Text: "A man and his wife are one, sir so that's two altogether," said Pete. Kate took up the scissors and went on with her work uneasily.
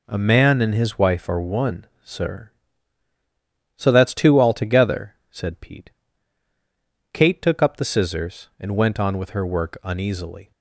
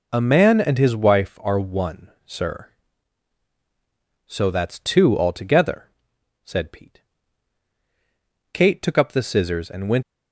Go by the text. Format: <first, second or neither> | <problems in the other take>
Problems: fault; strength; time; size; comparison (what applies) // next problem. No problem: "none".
first | stops before "on with her work uneasily"; at 10.0 s